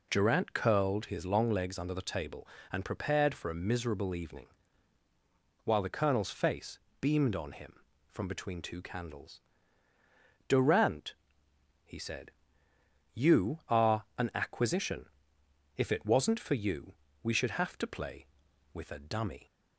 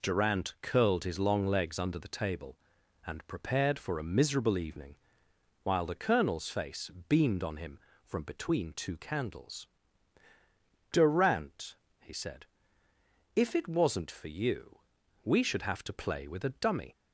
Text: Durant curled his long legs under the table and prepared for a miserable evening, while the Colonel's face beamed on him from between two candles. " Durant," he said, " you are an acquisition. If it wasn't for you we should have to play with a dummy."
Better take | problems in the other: first | pauses between "face" and "beamed"; slight; at 6.8 s; 0.18 s long; slight in the first // skips "you are an acquisition"; at 13.3 s // pauses between "you" and "we"; at 14.7 s; 0.44 s long; slight in the first

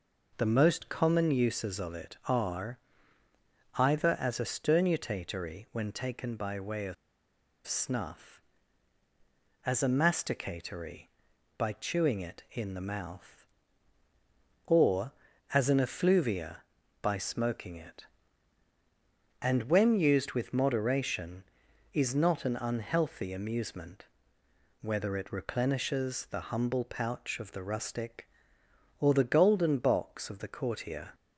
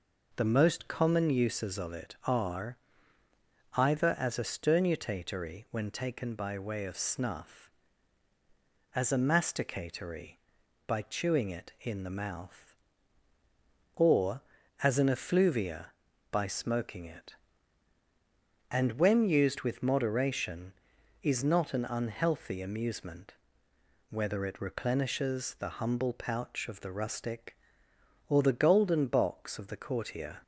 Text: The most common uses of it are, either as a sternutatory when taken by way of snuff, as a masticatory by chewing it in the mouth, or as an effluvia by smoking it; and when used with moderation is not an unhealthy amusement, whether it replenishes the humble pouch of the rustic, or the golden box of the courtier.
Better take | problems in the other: second | pauses between "of" and "snuff"; noticeable; at 6.9 s; 0.72 s long

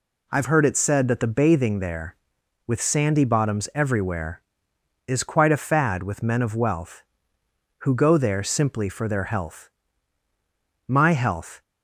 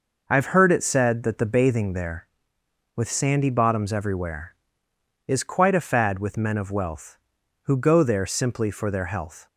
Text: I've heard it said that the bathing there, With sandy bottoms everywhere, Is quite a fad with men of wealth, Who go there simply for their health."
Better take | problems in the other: second | goes on to say "My health"; noticeable; from 10.8 s on; 0.76 s long

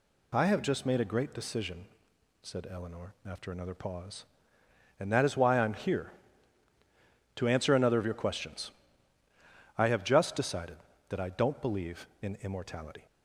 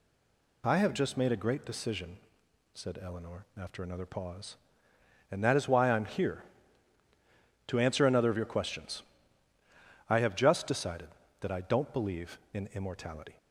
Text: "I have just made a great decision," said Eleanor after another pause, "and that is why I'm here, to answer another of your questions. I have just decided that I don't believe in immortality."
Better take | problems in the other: first | stays silent before the first word; slight; until 0.6 s; 0.6 s long

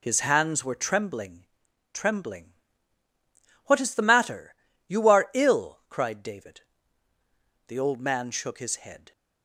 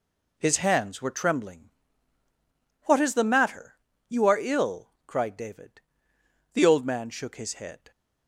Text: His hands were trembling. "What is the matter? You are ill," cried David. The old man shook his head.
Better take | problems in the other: second | says "trembling" twice; at 1.9 s

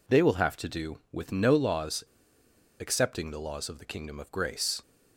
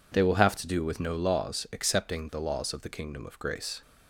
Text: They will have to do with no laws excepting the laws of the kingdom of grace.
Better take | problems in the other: second | pauses between "laws" and "excepting"; noticeable; at 2.0 s; 0.75 s long

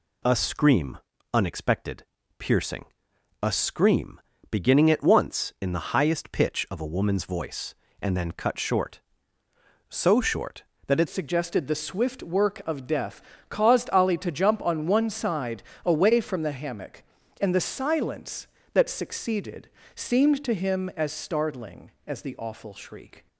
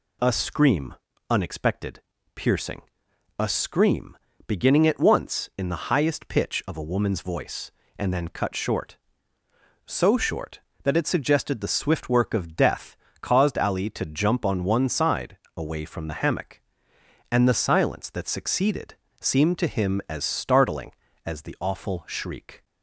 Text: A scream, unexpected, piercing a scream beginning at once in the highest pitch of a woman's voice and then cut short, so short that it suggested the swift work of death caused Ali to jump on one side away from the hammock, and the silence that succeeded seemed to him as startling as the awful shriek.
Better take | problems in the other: second | pauses between "piercing" and "a"; noticeable; at 2.8 s; 0.56 s long; noticeable in the second // pauses between "scream" and "beginning"; slight; at 4.2 s; 0.28 s long; slight in the second // changes voice at "suggested"; from 11.0 s on; 12.2 s long // pauses between "death" and "caused"; slight; at 13.2 s; 0.26 s long; slight in the second // pauses between "side" and "away"; slight; at 15.6 s; 0.24 s long; slight in the second // pauses between "succeeded" and "seemed"; slight; at 19.6 s; 0.26 s long; slight in the second

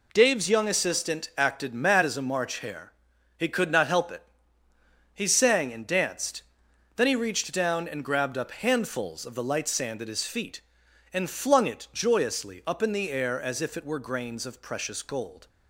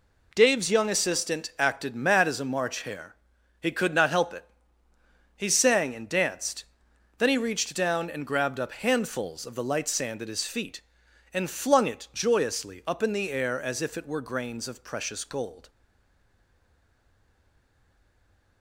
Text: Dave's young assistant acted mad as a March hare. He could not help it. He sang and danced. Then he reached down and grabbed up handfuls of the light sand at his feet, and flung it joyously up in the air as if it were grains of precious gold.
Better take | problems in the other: first | stays silent after the last word; strong; from 15.6 s on; 3.0 s long

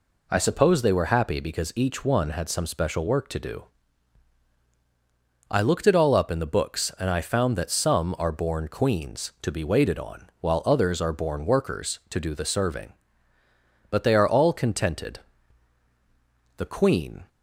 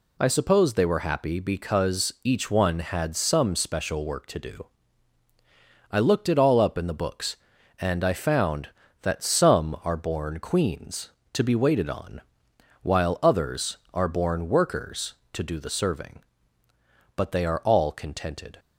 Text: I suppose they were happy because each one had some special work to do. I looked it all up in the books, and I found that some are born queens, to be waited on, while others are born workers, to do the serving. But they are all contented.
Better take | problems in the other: second | goes on to say "The queen"; noticeable; from 16.5 s on; 0.70 s long

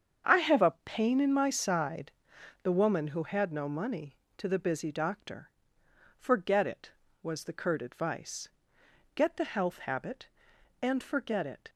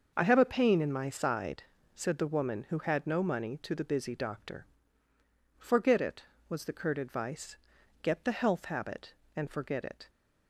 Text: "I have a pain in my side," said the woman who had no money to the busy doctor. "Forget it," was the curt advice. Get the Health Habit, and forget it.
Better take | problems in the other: second | starts louder than the rest; strong; until 1.4 s; 7.5 dB; also in the second // skips "said"; at 2.3 s

